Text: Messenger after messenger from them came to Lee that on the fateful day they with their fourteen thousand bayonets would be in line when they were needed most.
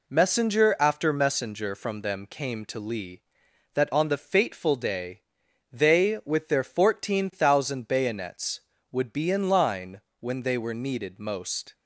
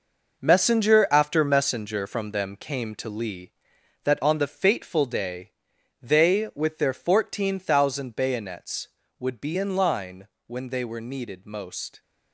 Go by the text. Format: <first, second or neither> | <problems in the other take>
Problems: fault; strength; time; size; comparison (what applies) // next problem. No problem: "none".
first | gets quieter; strong; throughout; 10 dB // pauses between "day" and "they"; noticeable; at 5.5 s; 0.50 s long; noticeable in the first // pauses between "line" and "when"; slight; at 10.2 s; 0.18 s long; slight in the first